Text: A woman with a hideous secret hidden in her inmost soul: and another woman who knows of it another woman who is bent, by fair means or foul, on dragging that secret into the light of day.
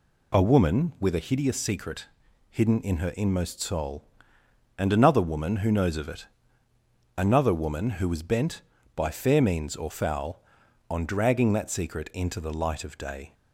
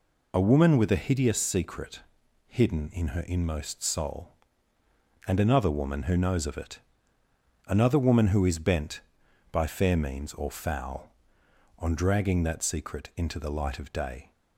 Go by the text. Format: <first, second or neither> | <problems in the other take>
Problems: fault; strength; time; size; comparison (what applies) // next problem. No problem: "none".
second | pauses between "secret" and "hidden"; at 2.0 s; 0.42 s long; also in the second // pauses between "it" and "another"; noticeable; at 6.2 s; 0.90 s long; noticeable in the second // says "was" for "is"; at 8.0 s